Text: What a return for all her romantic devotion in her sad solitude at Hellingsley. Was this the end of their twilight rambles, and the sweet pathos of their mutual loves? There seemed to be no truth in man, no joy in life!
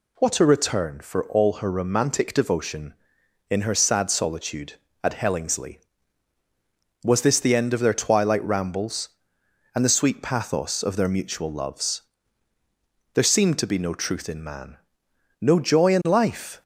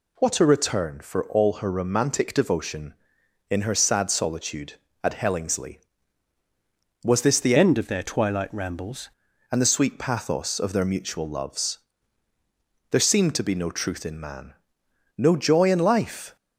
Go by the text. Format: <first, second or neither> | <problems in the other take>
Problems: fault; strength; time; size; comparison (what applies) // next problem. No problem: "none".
first | changes voice from "end" to "rambles"; from 7.5 to 9.1 s; 1.6 s long